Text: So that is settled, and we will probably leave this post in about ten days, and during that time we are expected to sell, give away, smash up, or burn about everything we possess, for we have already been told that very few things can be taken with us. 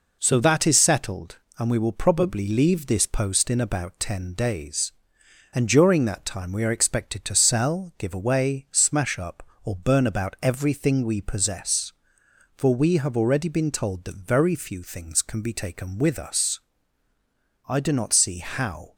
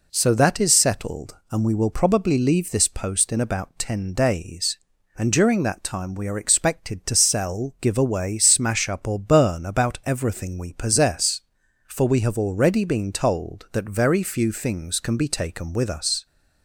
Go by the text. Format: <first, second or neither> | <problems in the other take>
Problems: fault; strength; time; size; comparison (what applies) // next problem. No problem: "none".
second | goes on to say "I do not see how"; noticeable; from 17.6 s on; 1.2 s long